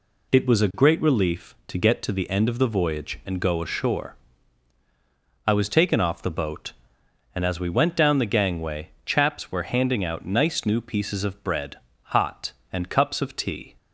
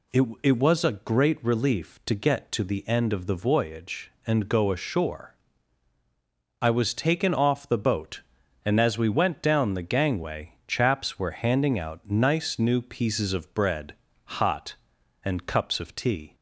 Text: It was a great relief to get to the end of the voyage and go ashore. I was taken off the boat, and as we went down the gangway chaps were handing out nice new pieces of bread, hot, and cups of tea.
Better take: first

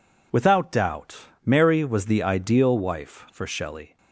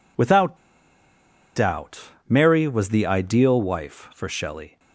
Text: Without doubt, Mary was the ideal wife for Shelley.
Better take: first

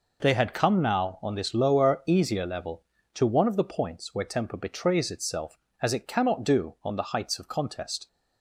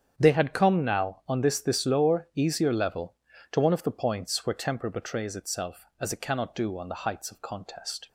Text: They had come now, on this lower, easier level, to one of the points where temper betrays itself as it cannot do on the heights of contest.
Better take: first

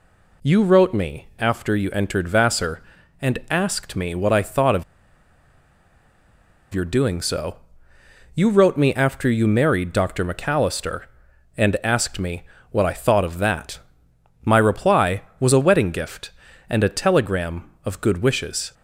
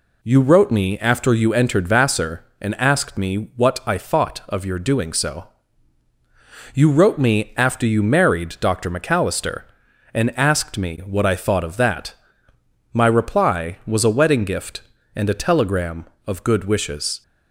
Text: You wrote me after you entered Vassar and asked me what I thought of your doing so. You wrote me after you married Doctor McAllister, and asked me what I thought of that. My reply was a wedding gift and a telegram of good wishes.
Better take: second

